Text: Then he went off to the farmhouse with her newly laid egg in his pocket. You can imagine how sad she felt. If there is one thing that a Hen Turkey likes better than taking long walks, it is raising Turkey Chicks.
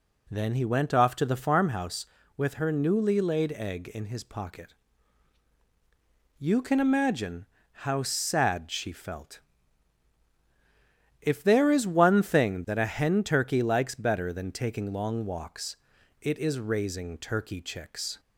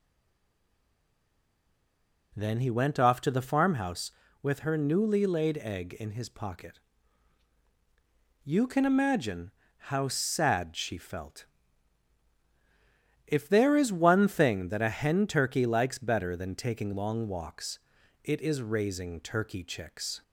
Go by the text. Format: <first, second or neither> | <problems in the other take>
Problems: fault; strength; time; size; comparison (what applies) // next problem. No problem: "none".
first | stays silent before the first word; until 2.3 s; 2.3 s long // pauses between "imagine" and "how"; slight; at 9.5 s; 0.26 s long; slight in the first